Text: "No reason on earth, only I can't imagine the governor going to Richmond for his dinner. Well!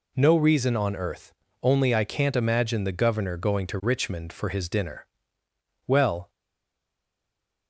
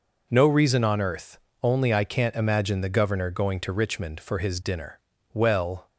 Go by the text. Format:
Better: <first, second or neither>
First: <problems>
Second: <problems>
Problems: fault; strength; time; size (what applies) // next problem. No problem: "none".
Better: second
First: stays silent after the last word; noticeable; from 6.2 s on; 1.4 s long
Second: none